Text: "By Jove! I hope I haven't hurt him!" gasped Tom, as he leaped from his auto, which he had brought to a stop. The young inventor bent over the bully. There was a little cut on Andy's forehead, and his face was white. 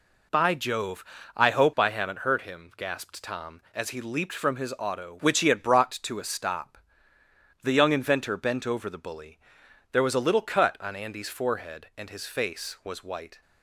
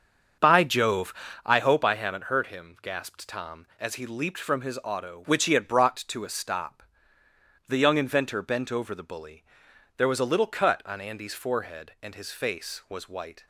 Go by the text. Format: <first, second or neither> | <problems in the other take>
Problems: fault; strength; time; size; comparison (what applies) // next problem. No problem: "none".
first | starts louder than the rest; until 1.5 s; 7 dB